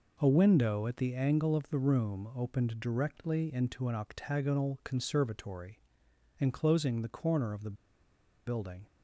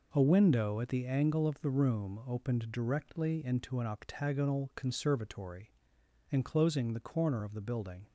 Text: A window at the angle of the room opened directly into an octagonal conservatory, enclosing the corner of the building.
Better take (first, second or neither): second